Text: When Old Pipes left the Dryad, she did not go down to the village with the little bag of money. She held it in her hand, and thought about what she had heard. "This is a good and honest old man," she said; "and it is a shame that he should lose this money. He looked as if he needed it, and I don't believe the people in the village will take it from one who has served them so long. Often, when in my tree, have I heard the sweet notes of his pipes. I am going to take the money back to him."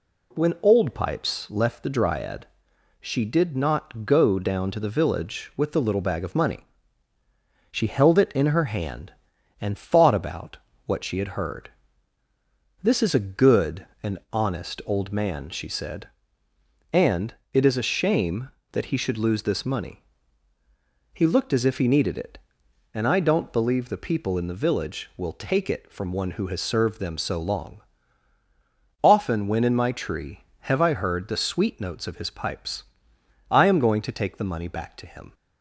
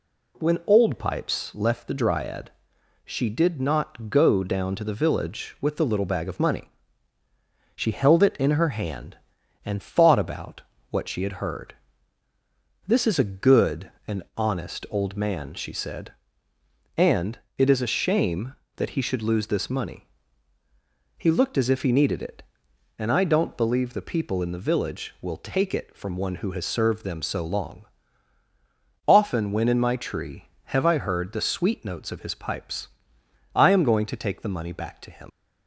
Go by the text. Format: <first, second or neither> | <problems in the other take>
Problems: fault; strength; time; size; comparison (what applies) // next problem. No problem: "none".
first | pauses between "about" and "what"; slight; at 10.6 s; 0.28 s long; slight in the first // pauses between "and" and "honest"; slight; at 14.2 s; 0.16 s long; slight in the first // pauses between "and" and "it"; slight; at 17.3 s; 0.20 s long; slight in the first // leaves "him" unfinished; at 35.2 s; 80 ms